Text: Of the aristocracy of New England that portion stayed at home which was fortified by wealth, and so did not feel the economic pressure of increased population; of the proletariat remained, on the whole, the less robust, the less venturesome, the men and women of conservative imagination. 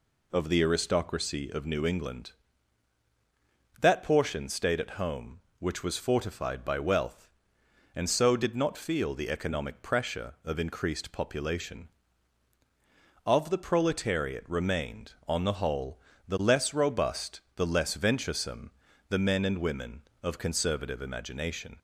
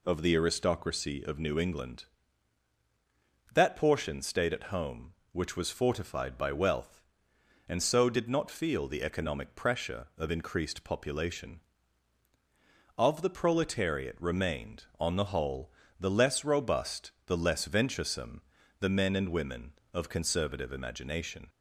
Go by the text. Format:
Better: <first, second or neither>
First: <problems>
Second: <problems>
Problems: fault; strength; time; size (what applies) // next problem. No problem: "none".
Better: neither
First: none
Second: none